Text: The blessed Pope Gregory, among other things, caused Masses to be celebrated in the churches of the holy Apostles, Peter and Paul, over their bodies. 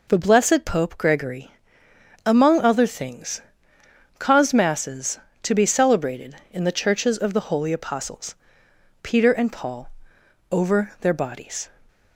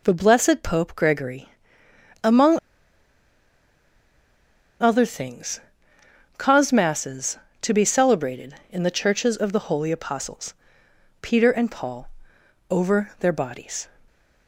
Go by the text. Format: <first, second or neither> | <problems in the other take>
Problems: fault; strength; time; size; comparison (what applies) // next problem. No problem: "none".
first | pauses between "among" and "other"; strong; at 2.5 s; 2.2 s long